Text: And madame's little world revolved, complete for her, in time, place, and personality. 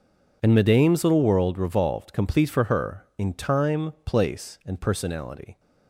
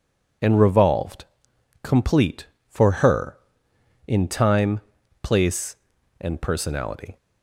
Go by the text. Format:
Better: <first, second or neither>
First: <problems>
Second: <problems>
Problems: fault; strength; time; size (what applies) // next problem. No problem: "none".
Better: first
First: none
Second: skips "madame's little world"; at 0.6 s